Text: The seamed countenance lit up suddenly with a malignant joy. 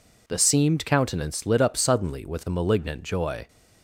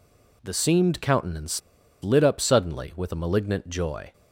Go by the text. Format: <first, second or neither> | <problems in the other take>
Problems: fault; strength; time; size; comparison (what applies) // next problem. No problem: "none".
first | pauses between "countenance" and "lit"; at 1.6 s; 0.42 s long